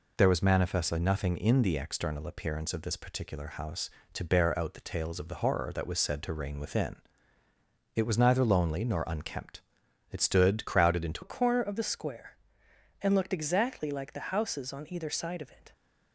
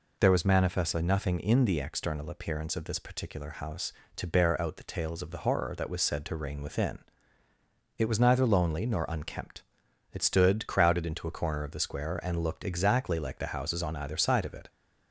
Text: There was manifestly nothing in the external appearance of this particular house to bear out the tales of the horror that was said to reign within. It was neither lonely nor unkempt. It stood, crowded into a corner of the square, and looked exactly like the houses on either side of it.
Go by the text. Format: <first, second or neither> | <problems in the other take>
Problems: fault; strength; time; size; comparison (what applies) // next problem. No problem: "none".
second | changes voice at "a"; from 11.2 s on; 4.5 s long